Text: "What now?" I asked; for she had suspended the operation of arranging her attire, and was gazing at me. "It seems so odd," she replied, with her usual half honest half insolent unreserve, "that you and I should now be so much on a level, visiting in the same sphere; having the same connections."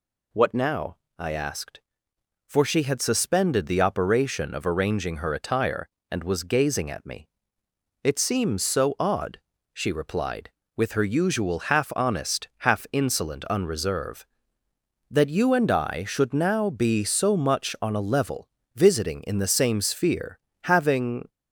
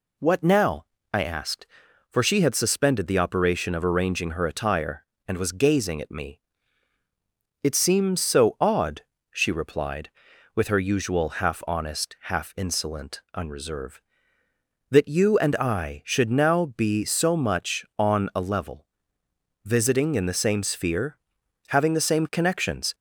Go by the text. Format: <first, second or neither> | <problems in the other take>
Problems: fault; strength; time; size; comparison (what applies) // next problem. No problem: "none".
second | stops before "the same connections"; at 21.2 s